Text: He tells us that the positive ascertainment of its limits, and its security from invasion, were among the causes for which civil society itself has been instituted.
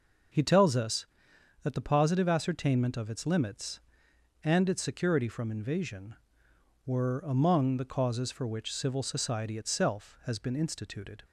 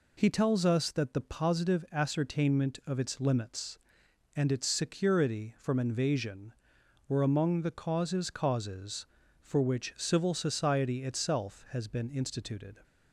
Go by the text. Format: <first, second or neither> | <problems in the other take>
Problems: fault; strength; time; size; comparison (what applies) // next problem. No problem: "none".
first | says "causes" twice; at 8.3 s